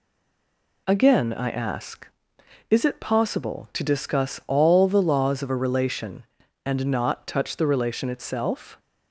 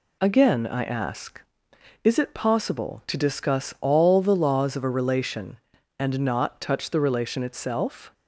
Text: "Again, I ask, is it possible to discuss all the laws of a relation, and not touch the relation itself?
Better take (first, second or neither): second